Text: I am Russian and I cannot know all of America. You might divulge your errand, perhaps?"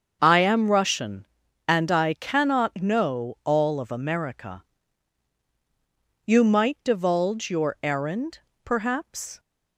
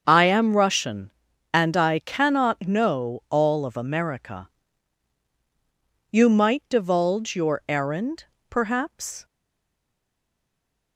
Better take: first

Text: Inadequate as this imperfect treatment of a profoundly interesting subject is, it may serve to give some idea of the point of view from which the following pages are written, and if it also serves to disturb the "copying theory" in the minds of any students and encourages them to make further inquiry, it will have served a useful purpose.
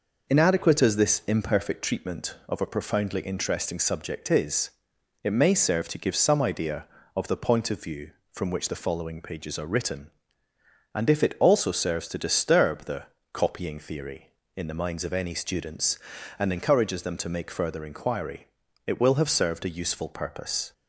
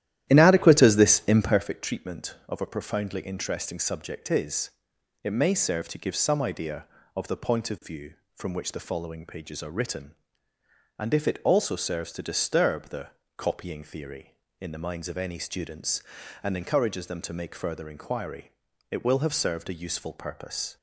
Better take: first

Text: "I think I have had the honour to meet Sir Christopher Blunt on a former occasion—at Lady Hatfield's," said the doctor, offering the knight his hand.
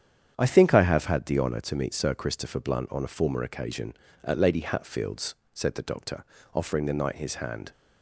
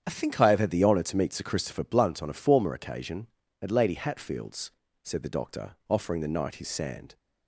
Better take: first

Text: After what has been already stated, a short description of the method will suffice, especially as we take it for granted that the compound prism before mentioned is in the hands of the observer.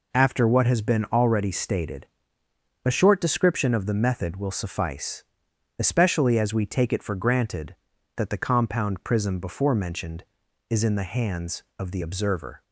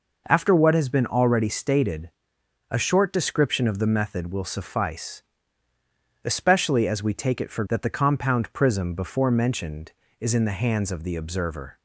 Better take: first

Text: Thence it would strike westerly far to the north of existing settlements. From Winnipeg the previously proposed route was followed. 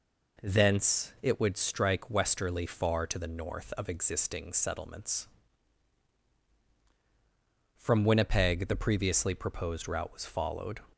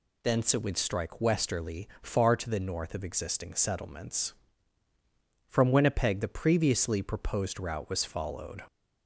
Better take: neither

